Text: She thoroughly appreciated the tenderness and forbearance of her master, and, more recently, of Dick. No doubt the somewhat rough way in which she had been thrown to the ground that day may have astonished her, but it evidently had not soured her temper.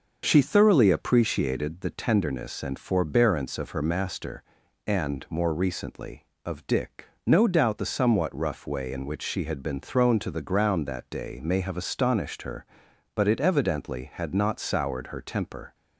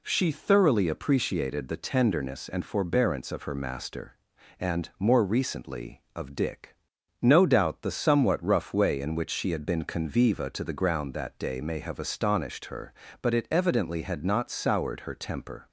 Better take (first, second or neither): first